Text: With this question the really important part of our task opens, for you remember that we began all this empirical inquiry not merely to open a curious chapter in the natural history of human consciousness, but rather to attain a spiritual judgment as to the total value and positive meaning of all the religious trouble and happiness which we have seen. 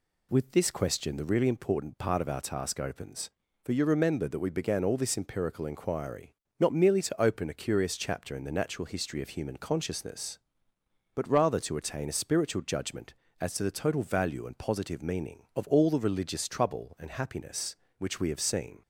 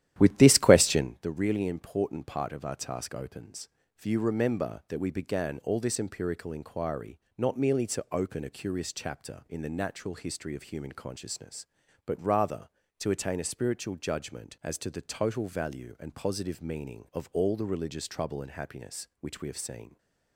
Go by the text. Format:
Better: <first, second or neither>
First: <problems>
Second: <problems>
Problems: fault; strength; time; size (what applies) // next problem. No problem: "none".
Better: first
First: pauses between "inquiry" and "not"; slight; at 6.3 s; 0.24 s long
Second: starts louder than the rest; strong; until 1.2 s; 12 dB // pauses between "inquiry" and "not"; slight; at 7.1 s; 0.18 s long